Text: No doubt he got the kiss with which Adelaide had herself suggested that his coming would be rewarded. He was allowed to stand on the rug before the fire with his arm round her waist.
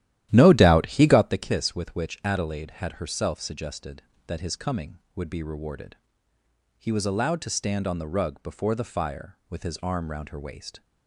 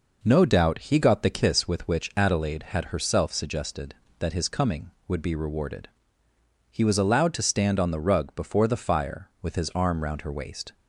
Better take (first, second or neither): second